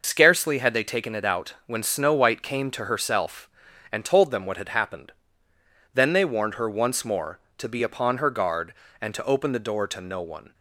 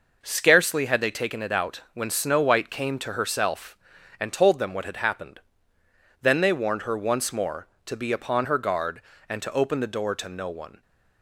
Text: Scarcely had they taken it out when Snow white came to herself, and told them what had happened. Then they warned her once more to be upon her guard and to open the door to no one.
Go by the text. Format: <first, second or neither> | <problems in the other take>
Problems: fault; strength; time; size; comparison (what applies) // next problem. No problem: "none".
second | loses the start of "Scarcely"; at 0.0 s; 85 ms